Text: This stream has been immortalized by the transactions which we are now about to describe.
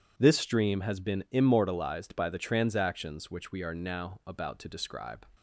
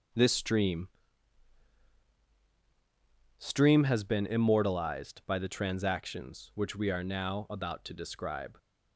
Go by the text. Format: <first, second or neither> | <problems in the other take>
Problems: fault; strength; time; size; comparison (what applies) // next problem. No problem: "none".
first | says "stream" twice; at 3.3 s